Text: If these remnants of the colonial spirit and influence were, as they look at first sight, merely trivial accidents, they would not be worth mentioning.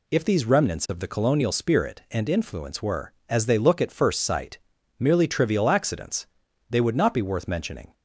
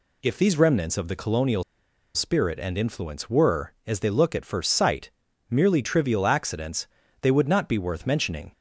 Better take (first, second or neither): first